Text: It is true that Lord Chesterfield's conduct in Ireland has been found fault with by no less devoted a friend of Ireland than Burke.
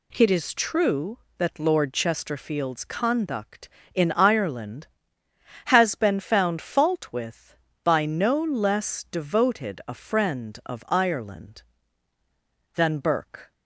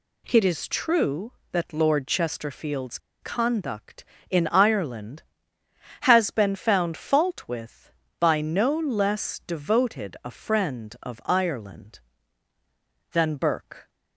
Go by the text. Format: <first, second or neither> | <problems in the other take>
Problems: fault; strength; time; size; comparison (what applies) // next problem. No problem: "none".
first | pauses between "Chesterfield's" and "conduct"; slight; at 2.9 s; 0.24 s long